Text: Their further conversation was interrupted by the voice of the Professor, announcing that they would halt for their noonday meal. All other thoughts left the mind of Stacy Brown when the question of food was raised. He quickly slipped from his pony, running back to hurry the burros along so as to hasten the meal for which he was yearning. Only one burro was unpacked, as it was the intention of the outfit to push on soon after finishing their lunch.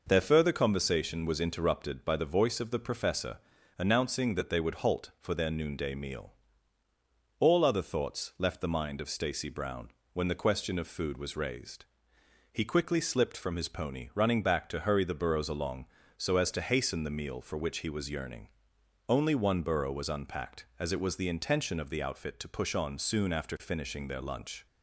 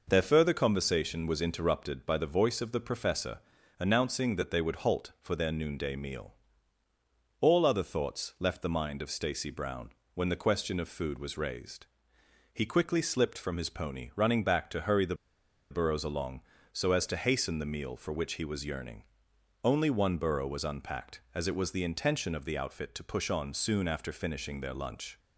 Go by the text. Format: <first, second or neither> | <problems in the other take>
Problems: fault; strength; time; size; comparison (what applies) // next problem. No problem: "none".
first | pauses between "Brown" and "when"; slight; at 9.9 s; 0.24 s long; slight in the first // pauses between "the" and "burros"; noticeable; at 15.1 s; 0.56 s long